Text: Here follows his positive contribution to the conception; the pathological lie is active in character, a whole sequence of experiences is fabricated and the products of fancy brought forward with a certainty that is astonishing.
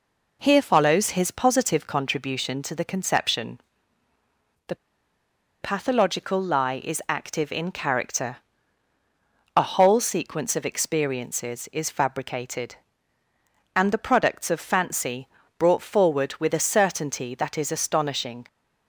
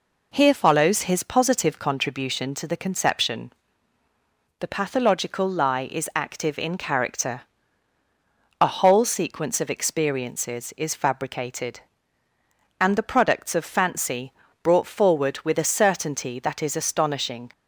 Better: second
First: pauses between "the" and "pathological"; noticeable; at 4.7 s; 0.87 s long // pauses between "fancy" and "brought"; slight; at 15.2 s; 0.30 s long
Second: pauses between "fancy" and "brought"; slight; at 14.3 s; 0.30 s long

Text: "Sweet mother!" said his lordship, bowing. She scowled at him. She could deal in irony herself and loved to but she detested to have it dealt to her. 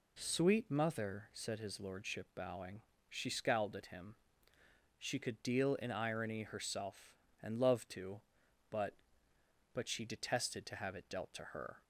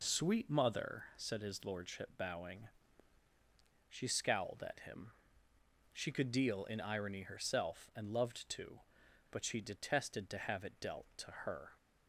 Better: second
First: says "but" twice; at 9.7 s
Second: none

